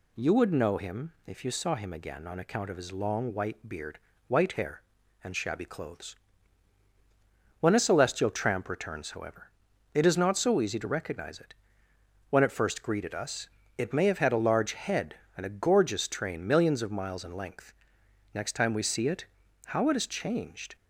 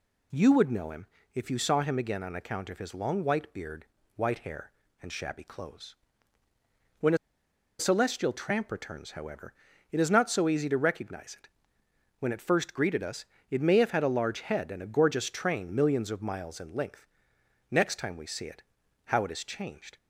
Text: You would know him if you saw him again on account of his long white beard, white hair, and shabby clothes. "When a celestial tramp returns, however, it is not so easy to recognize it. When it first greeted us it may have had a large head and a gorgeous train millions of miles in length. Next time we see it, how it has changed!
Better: first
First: pauses between "us" and "it"; slight; at 13.4 s; 0.30 s long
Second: pauses between "him" and "if"; slight; at 1.0 s; 0.28 s long // pauses between "a" and "celestial"; noticeable; at 7.1 s; 0.62 s long // pauses between "us" and "it"; slight; at 13.2 s; 0.24 s long

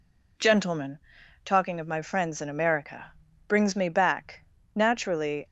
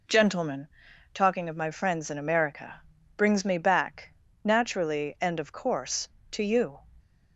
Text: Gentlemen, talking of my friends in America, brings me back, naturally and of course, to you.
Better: second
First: stops before "and of course to you"; at 5.4 s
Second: none

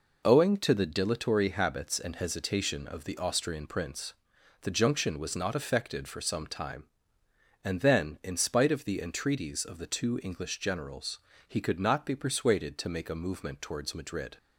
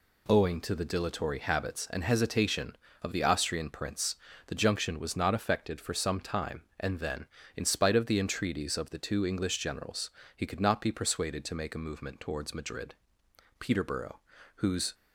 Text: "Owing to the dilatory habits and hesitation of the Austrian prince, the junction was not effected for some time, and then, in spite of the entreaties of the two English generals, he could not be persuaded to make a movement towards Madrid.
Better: first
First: none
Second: goes on to say "Peterborough whose"; from 13.6 s on; 1.3 s long

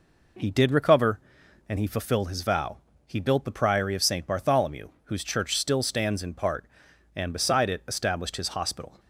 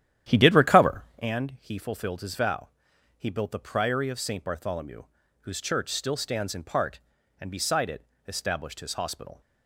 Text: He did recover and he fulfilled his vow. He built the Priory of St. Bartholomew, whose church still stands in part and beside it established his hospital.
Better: first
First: none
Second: starts louder than the rest; strong; until 1.3 s; 11 dB // pauses between "it" and "established"; slight; at 8.0 s; 0.22 s long

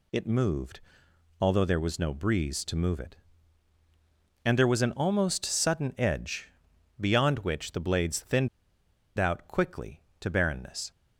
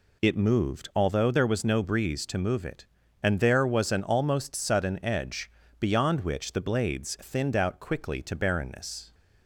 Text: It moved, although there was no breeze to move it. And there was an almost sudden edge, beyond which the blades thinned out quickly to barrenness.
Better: second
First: pauses between "thinned" and "out"; noticeable; at 8.4 s; 0.70 s long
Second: none

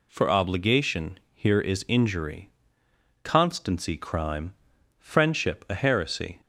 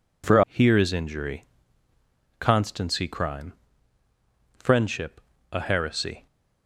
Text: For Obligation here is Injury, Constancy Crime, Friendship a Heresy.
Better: first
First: none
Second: skips "Obligation"; at 0.4 s // pauses between "Friendship" and "a"; slight; at 5.2 s; 0.32 s long

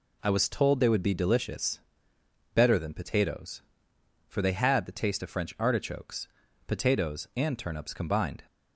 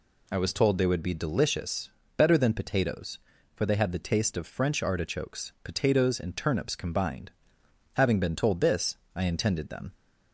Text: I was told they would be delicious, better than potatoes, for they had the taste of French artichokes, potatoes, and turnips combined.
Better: first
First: none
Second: goes on to say "Having been told this I intended them"; strong; from 7.9 s on; 2.0 s long

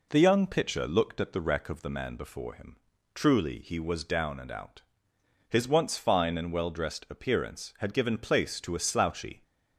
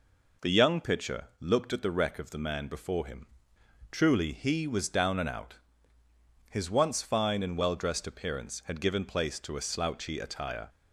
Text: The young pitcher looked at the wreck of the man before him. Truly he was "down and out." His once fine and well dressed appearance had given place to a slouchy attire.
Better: second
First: stops before "attire"; at 9.4 s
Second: none

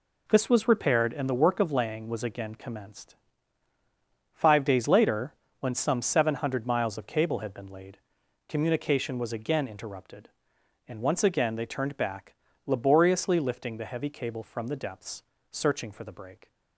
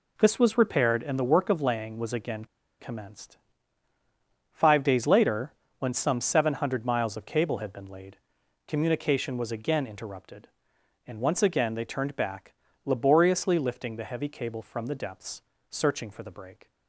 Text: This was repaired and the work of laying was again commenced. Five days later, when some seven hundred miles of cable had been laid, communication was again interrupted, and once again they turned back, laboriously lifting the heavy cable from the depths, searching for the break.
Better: first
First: none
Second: pauses between "again" and "commenced"; slight; at 2.4 s; 0.33 s long

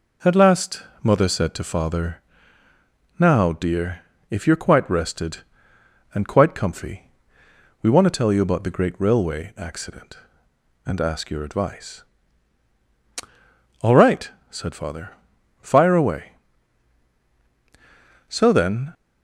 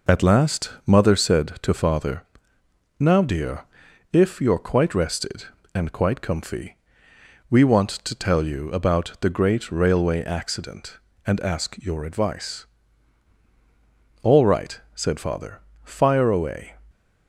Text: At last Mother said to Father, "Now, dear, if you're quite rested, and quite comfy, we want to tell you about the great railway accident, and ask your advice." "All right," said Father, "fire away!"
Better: second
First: pauses between "last" and "Mother"; slight; at 0.8 s; 0.18 s long // goes on to say "So then"; noticeable; from 18.2 s on; 0.66 s long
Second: pauses between "last" and "Mother"; slight; at 0.6 s; 0.16 s long

